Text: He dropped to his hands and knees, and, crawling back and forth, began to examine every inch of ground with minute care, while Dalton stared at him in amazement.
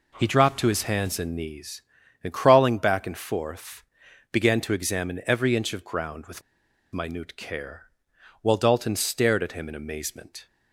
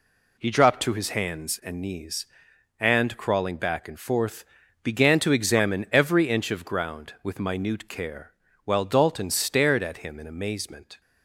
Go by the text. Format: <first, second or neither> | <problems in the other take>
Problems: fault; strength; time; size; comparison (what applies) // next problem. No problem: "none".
second | pauses between "with" and "minute"; noticeable; at 6.4 s; 0.52 s long